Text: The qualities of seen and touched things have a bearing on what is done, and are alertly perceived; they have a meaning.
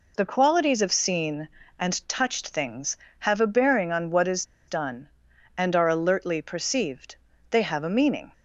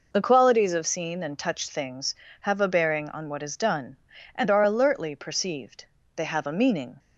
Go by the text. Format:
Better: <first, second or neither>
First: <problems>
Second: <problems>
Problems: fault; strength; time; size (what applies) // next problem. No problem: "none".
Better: second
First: pauses between "is" and "done"; slight; at 4.4 s; 0.23 s long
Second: none